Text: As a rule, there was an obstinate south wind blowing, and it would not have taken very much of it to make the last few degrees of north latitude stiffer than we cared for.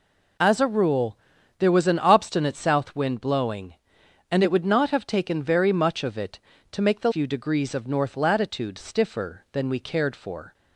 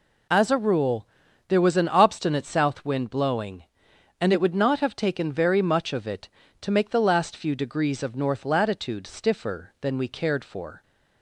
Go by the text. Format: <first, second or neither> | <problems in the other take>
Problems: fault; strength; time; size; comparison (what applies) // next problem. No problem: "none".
second | skips "last"; at 7.1 s